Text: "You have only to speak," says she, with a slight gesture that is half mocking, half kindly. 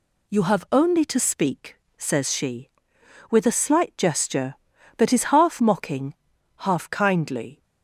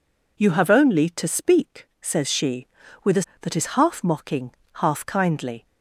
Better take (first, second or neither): first